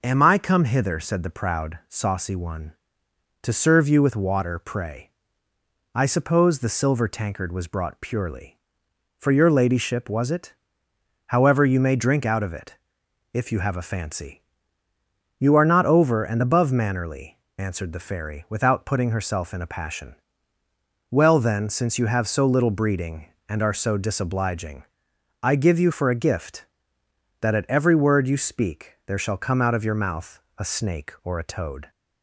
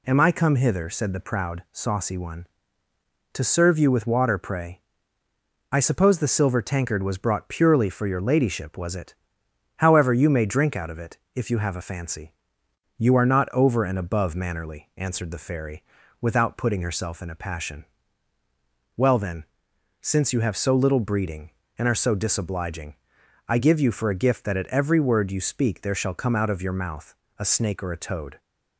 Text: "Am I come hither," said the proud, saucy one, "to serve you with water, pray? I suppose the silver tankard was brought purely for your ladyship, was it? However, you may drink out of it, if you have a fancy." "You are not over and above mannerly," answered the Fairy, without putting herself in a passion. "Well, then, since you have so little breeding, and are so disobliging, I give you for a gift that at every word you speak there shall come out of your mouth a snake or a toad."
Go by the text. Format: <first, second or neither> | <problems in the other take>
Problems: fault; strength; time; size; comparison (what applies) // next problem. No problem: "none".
neither | pauses between "mouth" and "a"; slight; the same in both